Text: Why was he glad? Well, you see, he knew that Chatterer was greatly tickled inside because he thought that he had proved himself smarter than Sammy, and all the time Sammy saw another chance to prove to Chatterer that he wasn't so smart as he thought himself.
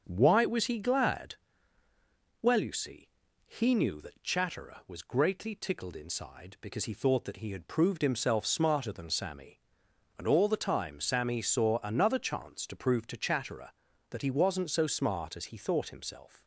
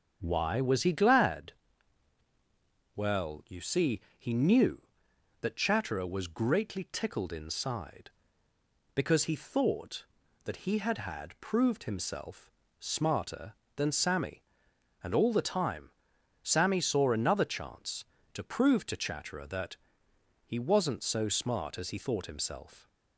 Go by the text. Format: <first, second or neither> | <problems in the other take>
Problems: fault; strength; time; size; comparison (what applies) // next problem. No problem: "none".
first | starts louder than the rest; until 1.2 s; 7 dB; also in the first // says "had" twice; at 10.9 s // pauses between "himself" and "smarter"; slight; at 12.5 s; 0.28 s long // pauses between "time" and "Sammy"; noticeable; at 15.8 s; 0.54 s long // pauses between "that" and "he"; noticeable; at 19.7 s; 0.70 s long